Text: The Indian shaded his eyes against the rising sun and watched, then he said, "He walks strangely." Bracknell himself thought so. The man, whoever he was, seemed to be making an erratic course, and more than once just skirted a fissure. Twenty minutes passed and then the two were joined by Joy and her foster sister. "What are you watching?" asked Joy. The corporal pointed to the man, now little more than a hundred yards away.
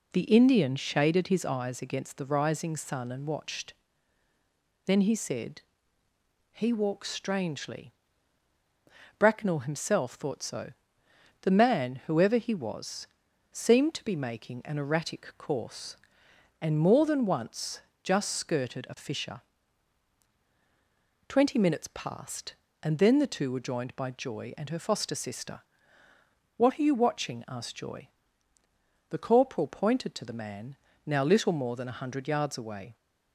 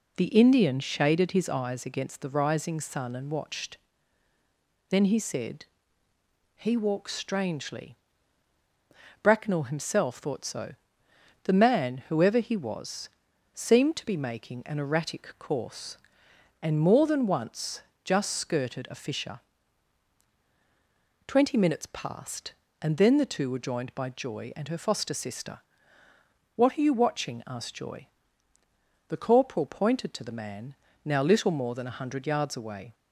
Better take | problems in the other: neither | pauses between "once" and "just"; slight; the same in both

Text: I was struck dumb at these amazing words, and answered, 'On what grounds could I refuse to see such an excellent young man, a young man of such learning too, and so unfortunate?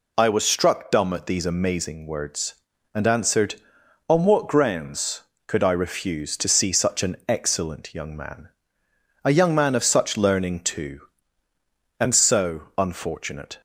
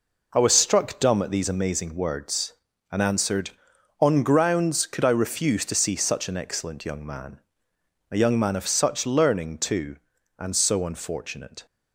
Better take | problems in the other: first | skips "what"; at 4.2 s

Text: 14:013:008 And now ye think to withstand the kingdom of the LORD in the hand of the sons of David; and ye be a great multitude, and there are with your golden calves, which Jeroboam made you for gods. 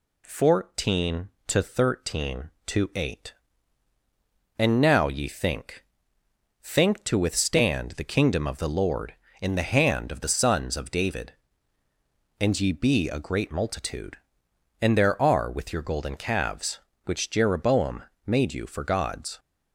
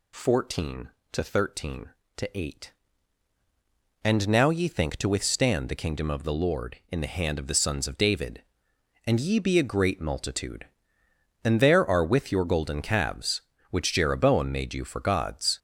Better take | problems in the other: second | says "think" twice; at 6.6 s // pauses between "Jeroboam" and "made"; slight; at 18.0 s; 0.22 s long

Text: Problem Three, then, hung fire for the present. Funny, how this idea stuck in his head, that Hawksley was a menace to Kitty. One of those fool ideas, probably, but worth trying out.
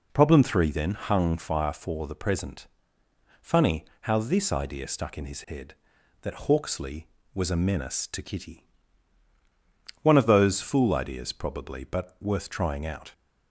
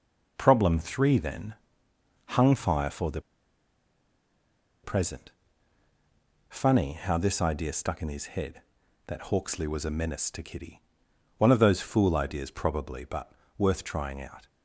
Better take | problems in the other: first | pauses between "the" and "present"; strong; at 3.2 s; 1.6 s long // pauses between "but" and "worth"; slight; at 13.3 s; 0.26 s long

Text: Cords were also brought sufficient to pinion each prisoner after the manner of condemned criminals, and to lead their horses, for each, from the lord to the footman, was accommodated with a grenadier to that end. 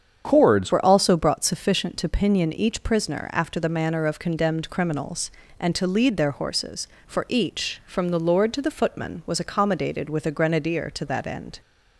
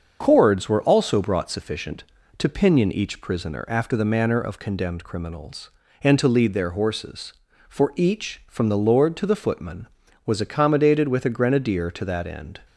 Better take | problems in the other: second | starts louder than the rest; strong; until 1.2 s; 7.5 dB; also in the second // changes voice at "were"; from 0.7 s on; 10.9 s long

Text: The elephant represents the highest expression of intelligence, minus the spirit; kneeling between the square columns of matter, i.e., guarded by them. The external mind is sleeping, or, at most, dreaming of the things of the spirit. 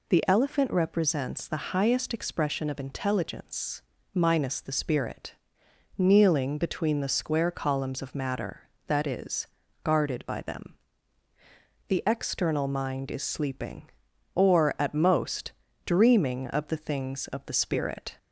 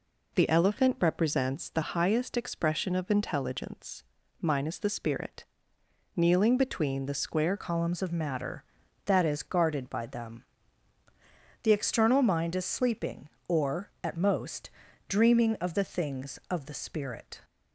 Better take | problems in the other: first | changes voice at "columns"; from 7.5 s on; 9.9 s long

